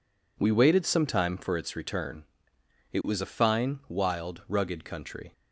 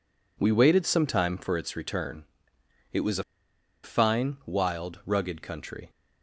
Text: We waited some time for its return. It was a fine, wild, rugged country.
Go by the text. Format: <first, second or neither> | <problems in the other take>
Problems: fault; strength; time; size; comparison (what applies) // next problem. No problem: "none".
first | pauses between "a" and "fine"; noticeable; at 3.2 s; 0.60 s long